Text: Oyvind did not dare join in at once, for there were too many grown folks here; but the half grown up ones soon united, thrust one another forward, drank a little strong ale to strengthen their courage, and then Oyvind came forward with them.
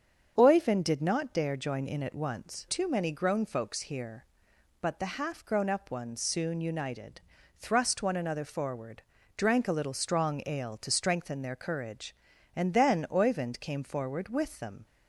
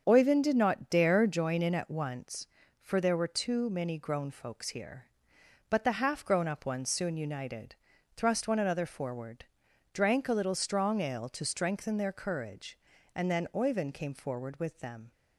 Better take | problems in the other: second | starts louder than the rest; strong; until 1.3 s; 7 dB; also in the second // skips "for there were"; at 2.6 s

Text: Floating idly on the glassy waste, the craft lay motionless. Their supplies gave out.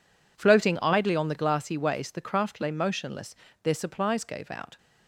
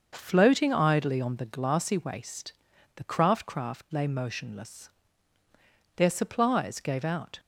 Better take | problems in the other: first | starts louder than the rest; until 1.1 s; 6.5 dB // says "craft" twice; at 3.4 s

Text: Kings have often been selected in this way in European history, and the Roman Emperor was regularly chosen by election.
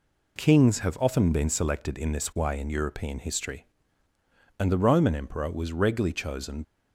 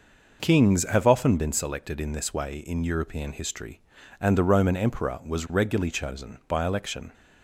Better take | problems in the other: second | stops before "by election"; at 6.6 s

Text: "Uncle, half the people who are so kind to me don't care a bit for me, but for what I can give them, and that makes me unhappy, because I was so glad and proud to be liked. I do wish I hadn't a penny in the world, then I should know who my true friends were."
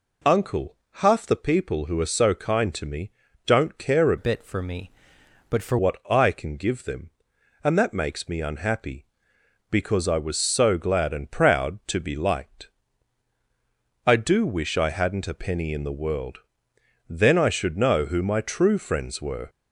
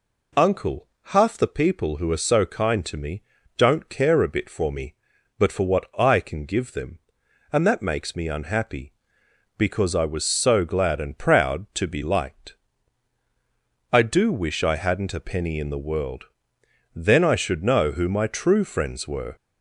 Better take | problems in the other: second | pauses between "me" and "don't"; slight; at 3.1 s; 0.34 s long; slight in the second // changes voice from "bit" to "for"; from 4.1 to 5.7 s; 1.6 s long

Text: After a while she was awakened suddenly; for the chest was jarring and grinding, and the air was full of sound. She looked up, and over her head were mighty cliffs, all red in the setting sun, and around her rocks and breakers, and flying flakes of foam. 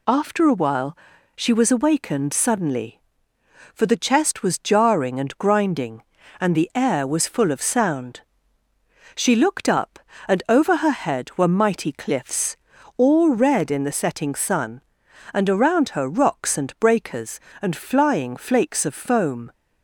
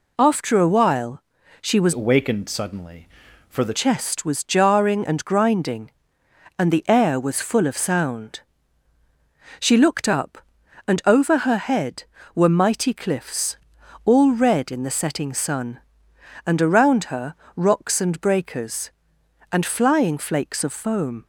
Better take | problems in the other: first | pauses between "while" and "she"; at 1.2 s; 0.40 s long; also in the first // changes voice from "awakened" to "the"; from 1.9 to 3.7 s; 1.8 s long // pauses between "her" and "rocks"; slight; at 17.3 s; 0.20 s long

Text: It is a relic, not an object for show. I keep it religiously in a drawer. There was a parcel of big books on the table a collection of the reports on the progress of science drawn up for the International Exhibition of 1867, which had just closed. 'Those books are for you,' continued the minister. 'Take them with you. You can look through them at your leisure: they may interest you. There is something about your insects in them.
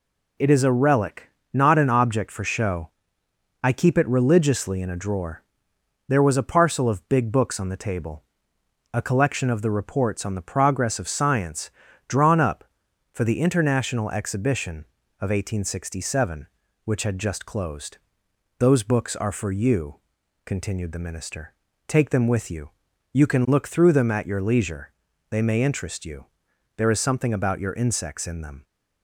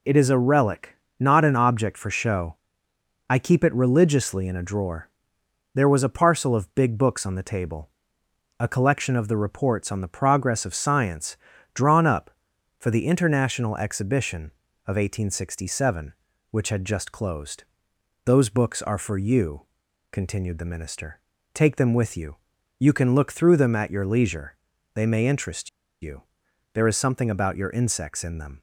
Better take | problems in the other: first | pauses between "table" and "a"; noticeable; at 7.8 s; 0.70 s long; noticeable in the first // pauses between "science" and "drawn"; at 11.3 s; 0.38 s long; also in the first // pauses between "interest" and "you"; slight; at 25.6 s; 0.33 s long

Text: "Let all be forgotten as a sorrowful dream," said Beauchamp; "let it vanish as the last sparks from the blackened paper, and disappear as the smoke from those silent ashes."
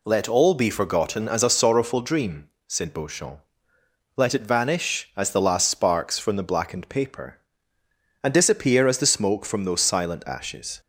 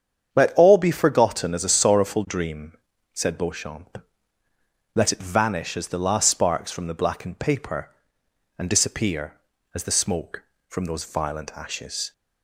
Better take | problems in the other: first | starts louder than the rest; strong; until 1.3 s; 8 dB // says "violent" for "silent"; at 11.0 s

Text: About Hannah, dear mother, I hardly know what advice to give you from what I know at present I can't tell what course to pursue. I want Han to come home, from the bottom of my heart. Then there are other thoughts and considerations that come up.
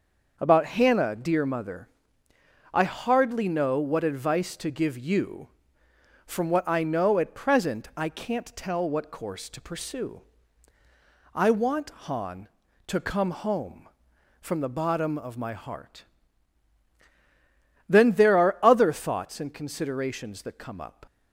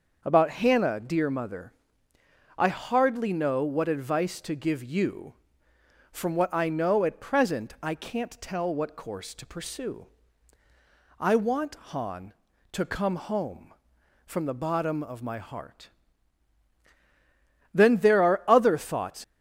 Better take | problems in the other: first | starts louder than the rest; noticeable; until 1.2 s; 6 dB; noticeable in the first // pauses between "want" and "Han"; slight; at 11.7 s; 0.16 s long; slight in the first // stops before "and considerations that come up"; at 19.2 s

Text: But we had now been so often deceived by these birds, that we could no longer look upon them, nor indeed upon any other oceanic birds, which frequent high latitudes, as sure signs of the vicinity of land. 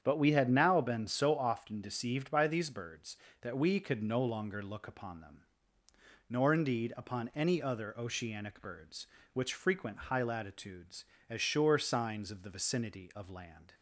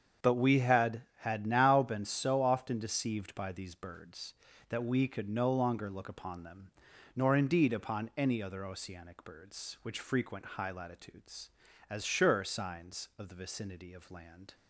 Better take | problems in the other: first | starts louder than the rest; strong; until 1.4 s; 7.5 dB; strong in the first // says "had" twice; at 1.2 s

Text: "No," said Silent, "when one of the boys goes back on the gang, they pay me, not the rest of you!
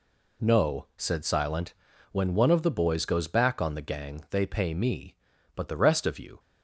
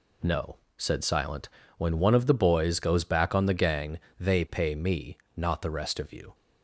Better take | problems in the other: second | says "but" for "not"; at 5.5 s

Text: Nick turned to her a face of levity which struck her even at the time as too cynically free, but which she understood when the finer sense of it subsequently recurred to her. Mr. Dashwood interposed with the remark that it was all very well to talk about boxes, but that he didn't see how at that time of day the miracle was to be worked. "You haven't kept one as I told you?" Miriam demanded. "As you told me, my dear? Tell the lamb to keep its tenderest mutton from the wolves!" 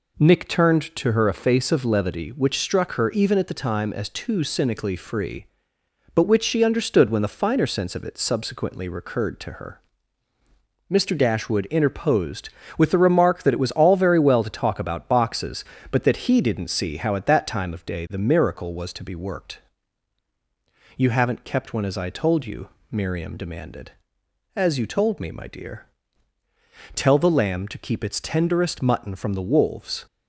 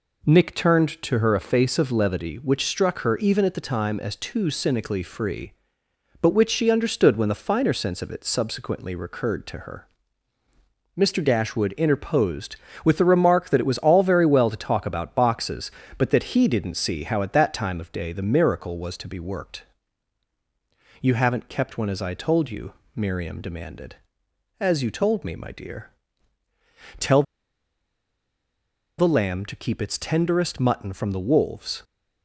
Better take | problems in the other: first | pauses between "Tell" and "the"; strong; at 27.2 s; 1.7 s long

